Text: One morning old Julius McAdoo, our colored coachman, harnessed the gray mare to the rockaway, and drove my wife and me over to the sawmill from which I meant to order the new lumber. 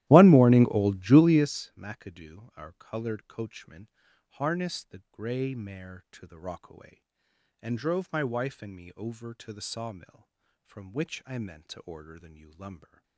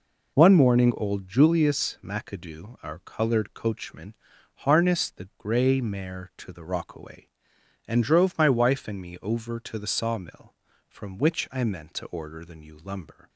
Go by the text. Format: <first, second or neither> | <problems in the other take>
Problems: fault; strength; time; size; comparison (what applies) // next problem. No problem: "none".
second | starts louder than the rest; strong; until 1.5 s; 15 dB